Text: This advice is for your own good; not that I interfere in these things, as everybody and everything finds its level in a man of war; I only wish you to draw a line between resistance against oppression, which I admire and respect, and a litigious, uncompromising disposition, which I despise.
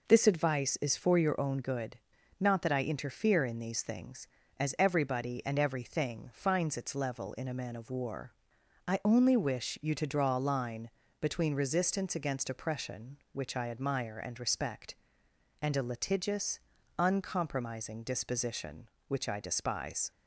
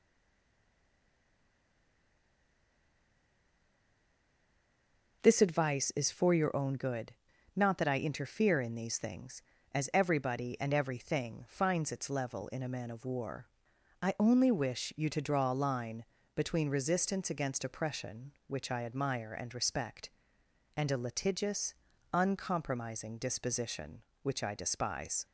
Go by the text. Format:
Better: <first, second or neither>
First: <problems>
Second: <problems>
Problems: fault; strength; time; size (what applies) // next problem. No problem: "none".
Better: first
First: pauses between "line" and "between"; slight; at 10.9 s; 0.30 s long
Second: stays silent before the first word; strong; until 5.2 s; 5.2 s long // pauses between "line" and "between"; slight; at 16.0 s; 0.30 s long